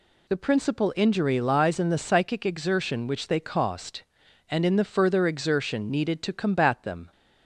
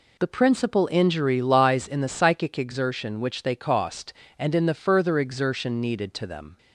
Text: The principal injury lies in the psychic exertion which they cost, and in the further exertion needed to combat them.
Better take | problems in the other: first | skips "combat"; at 6.2 s

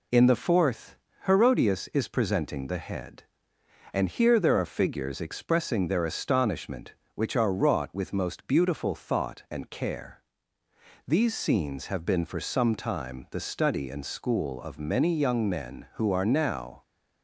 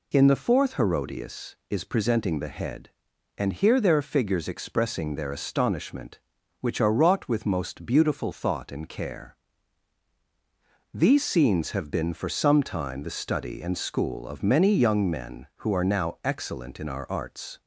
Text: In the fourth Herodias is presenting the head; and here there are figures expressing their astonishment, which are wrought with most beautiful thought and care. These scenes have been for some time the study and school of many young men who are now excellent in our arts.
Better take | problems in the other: second | pauses between "fourth" and "Herodias"; slight; at 0.9 s; 0.30 s long // stops before "excellent in our arts"; at 16.8 s

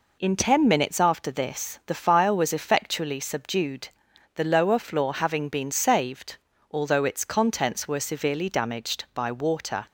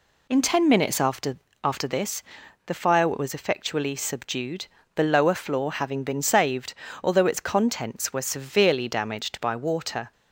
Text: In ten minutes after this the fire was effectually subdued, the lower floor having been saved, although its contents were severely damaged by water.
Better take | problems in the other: first | says "after" twice; at 1.6 s // pauses between "this" and "the"; at 2.2 s; 0.44 s long

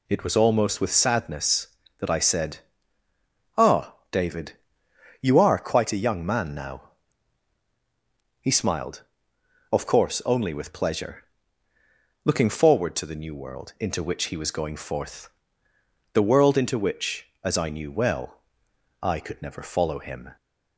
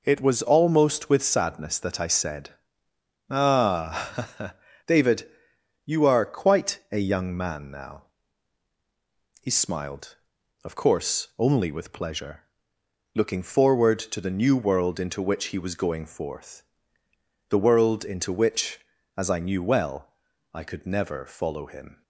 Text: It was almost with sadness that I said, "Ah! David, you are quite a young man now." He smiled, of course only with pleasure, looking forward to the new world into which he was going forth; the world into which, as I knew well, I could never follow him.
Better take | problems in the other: neither | none

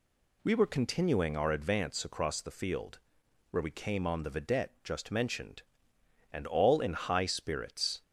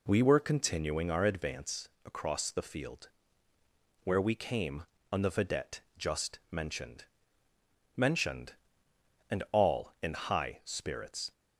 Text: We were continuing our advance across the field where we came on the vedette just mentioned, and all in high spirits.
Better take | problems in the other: first | pauses between "advance" and "across"; slight; at 1.8 s; 0.18 s long // pauses between "field" and "where"; noticeable; at 3.0 s; 0.96 s long; noticeable in the first // pauses between "vedette" and "just"; slight; at 5.7 s; 0.18 s long // says "mentioned" twice; at 7.9 s

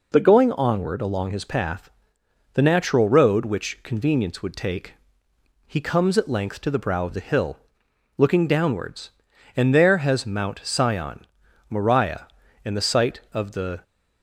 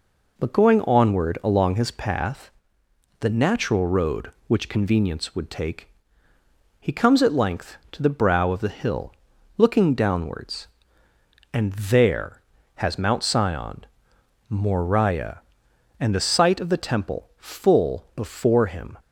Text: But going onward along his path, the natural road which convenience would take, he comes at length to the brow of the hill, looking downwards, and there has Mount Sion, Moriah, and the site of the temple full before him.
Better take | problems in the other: second | stops before "temple full before him"; at 13.8 s

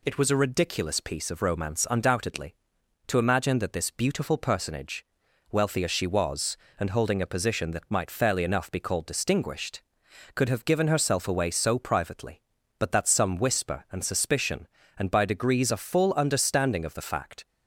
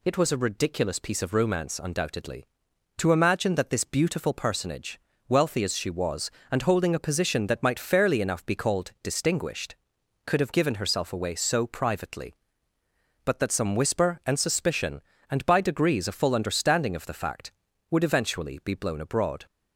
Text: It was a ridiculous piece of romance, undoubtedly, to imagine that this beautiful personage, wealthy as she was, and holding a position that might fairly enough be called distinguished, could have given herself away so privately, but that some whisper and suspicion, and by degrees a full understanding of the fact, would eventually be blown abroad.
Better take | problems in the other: second | stops before "would eventually be blown abroad"; at 17.4 s

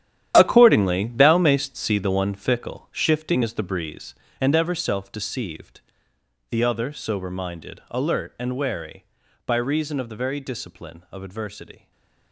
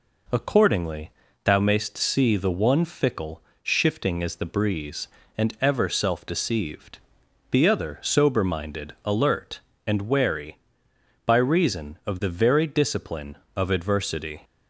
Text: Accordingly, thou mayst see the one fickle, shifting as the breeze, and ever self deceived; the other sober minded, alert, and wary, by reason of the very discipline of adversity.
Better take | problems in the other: second | gets quieter; strong; throughout; 12.5 dB // stays silent after the last word; slight; from 11.7 s on; 0.6 s long

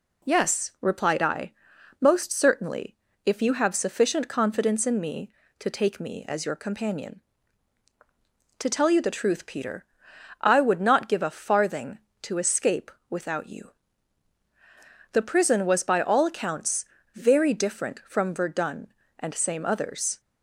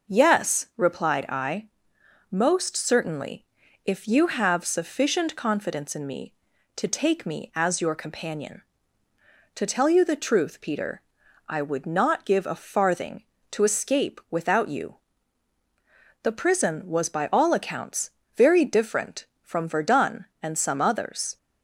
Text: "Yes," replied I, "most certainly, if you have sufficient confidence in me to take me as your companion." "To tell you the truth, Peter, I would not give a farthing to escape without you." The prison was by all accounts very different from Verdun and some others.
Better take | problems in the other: second | pauses between "escape" and "without"; slight; at 12.8 s; 0.20 s long // pauses between "accounts" and "very"; slight; at 16.8 s; 0.28 s long; slight in the second // says "same" for "some"; at 19.3 s

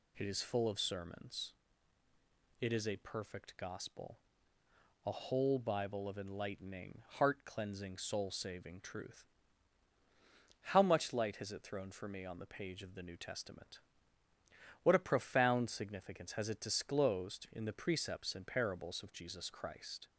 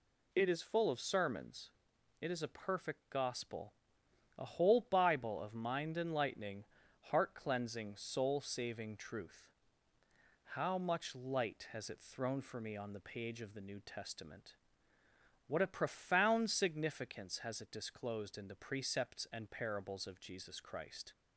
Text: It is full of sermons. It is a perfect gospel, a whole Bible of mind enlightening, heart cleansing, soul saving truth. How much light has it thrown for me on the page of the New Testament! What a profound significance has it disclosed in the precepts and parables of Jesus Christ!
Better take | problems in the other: second | skips "mind"; at 6.1 s

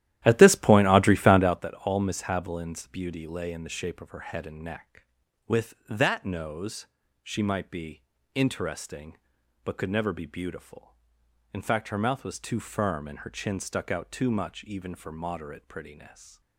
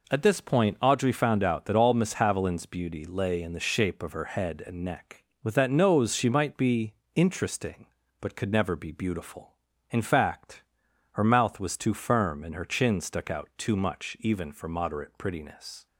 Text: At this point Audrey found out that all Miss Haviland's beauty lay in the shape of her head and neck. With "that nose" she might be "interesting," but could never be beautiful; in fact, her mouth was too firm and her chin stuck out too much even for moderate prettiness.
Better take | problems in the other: second | starts louder than the rest; strong; until 1.7 s; 13 dB // pauses between "nose" and "she"; slight; at 6.8 s; 0.36 s long // pauses between "be" and "interesting"; slight; at 8.0 s; 0.32 s long; slight in the second // stays silent after the last word; slight; from 16.0 s on; 0.5 s long

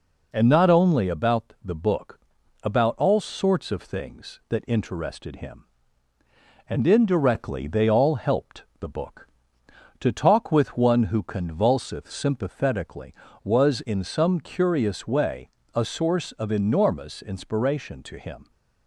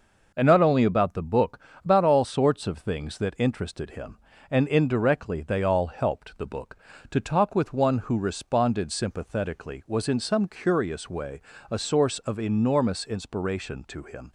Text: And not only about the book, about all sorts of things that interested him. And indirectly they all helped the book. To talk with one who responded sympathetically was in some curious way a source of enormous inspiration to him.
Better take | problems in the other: second | pauses between "helped" and "the"; slight; at 8.6 s; 0.16 s long // says "convulseth" for "responded"; at 11.2 s // pauses between "way" and "a"; slight; at 15.4 s; 0.26 s long; slight in the second

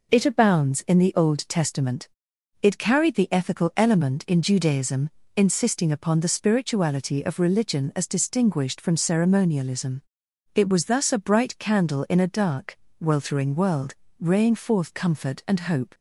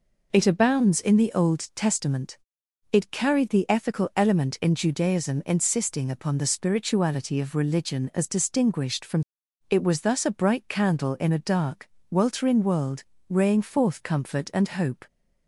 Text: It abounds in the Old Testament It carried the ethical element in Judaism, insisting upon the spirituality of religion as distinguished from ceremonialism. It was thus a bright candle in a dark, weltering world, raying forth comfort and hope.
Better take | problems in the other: first | pauses between "Testament" and "It"; noticeable; at 2.3 s; 0.54 s long; noticeable in the first // skips "ceremonialism"; at 9.4 s

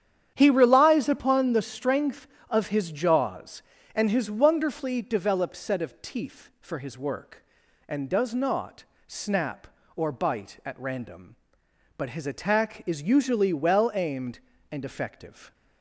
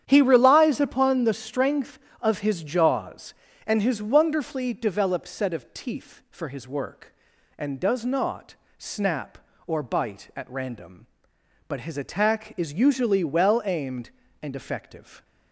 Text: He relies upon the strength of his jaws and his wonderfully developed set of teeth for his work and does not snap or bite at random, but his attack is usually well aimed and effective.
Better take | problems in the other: neither | starts louder than the rest; strong; the same in both // pauses between "not" and "snap"; slight; the same in both

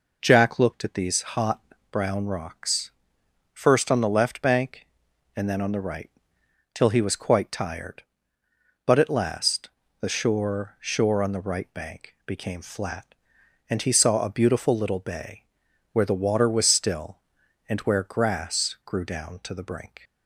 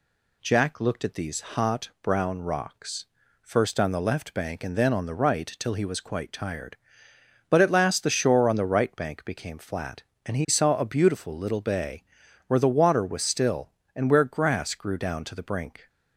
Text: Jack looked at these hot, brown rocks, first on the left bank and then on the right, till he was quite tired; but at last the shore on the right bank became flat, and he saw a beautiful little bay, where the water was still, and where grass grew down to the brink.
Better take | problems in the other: second | pauses between "last" and "the"; slight; at 9.7 s; 0.30 s long // says "shore" twice; at 10.7 s

